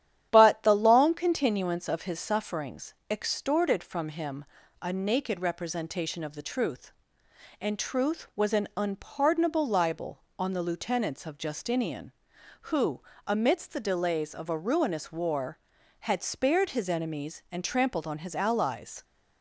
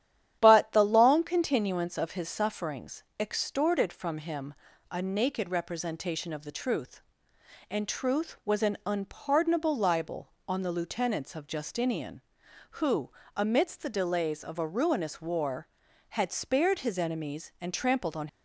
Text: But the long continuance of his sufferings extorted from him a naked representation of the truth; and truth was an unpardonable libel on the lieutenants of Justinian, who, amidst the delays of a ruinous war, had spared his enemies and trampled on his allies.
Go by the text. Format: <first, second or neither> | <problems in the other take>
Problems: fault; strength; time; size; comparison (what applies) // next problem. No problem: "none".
first | starts louder than the rest; strong; until 1.4 s; 10.5 dB; strong in the first // pauses between "sufferings" and "extorted"; slight; at 3.0 s; 0.16 s long; slight in the first // pauses between "him" and "a"; at 4.5 s; 0.38 s long; also in the first // stops before "his allies"; at 18.2 s